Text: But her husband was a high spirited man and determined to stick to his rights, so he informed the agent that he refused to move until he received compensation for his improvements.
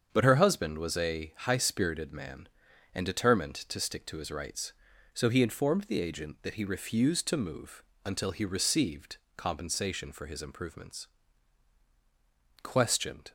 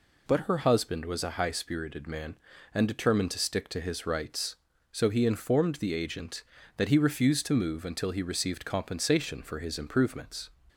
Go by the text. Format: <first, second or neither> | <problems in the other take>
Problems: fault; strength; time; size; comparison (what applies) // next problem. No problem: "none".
second | starts louder than the rest; strong; until 1.1 s; 7.5 dB // pauses between "move" and "until"; slight; at 7.8 s; 0.20 s long // pauses between "received" and "compensation"; slight; at 9.1 s; 0.18 s long // goes on to say "Questioned"; noticeable; from 12.6 s on; 0.70 s long